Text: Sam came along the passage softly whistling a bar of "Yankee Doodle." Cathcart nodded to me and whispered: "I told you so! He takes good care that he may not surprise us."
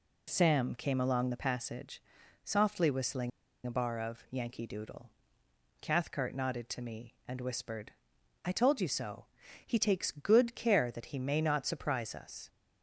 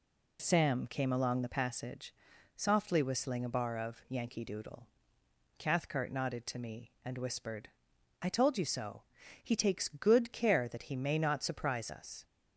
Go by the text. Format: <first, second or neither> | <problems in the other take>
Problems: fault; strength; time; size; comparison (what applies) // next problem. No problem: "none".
second | pauses between "passage" and "softly"; at 2.0 s; 0.42 s long; also in the second // pauses between "whistling" and "a"; at 3.3 s; 0.36 s long